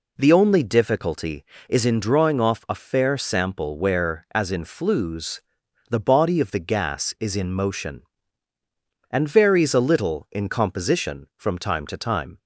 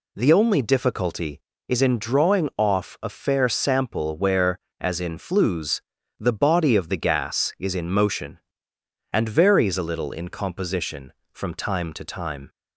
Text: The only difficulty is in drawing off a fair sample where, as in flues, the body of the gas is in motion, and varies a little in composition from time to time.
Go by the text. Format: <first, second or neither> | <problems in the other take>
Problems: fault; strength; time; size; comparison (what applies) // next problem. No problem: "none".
neither | none